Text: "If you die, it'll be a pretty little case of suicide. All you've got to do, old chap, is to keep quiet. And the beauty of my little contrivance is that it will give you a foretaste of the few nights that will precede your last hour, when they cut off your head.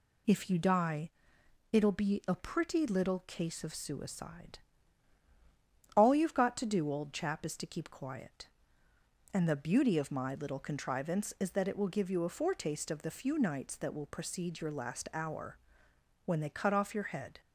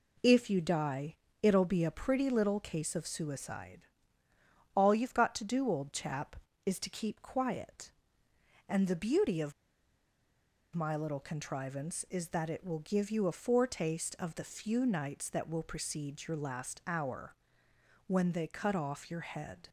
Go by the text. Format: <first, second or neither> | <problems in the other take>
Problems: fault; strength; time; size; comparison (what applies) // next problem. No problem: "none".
first | pauses between "of" and "my"; at 9.5 s; 1.2 s long